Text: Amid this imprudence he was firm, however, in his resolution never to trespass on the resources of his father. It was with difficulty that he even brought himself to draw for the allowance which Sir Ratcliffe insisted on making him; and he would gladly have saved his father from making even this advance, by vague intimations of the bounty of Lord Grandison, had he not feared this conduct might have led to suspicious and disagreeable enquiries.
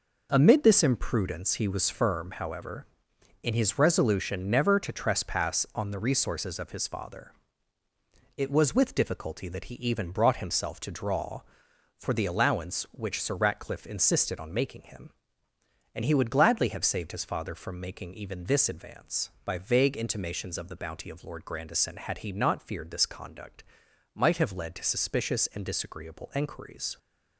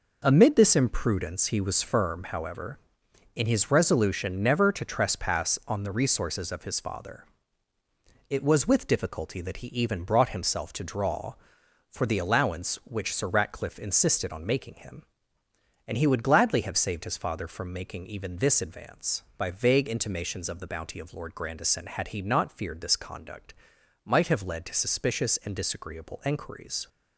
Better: neither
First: pauses between "conduct" and "might"; noticeable; at 23.6 s; 0.50 s long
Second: pauses between "conduct" and "might"; noticeable; at 23.5 s; 0.50 s long

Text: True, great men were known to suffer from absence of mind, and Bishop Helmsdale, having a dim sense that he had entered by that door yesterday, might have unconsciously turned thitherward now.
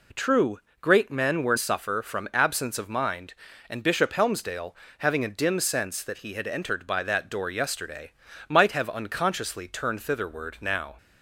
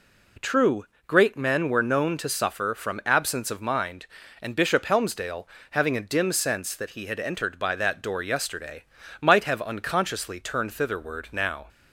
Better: second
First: skips "known to"; at 1.5 s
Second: none

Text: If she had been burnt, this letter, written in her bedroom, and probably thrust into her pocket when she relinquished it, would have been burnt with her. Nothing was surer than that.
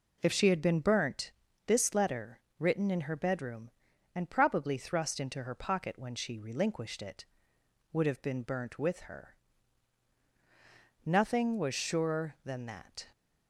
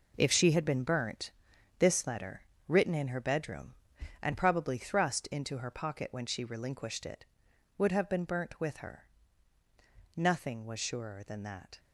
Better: first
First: none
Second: gets quieter; strong; throughout; 10 dB

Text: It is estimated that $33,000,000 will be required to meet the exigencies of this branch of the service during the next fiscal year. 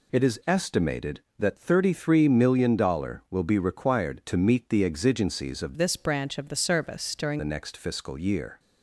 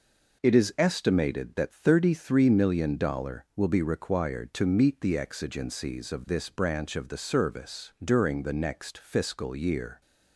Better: second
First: changes voice from "this" to "during"; from 5.7 to 7.4 s; 1.7 s long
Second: none

